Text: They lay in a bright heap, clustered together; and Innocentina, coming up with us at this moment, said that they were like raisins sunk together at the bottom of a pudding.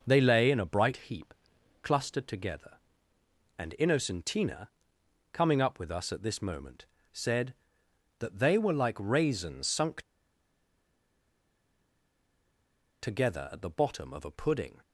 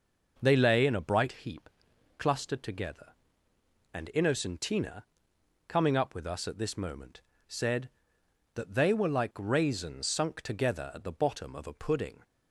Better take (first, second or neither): second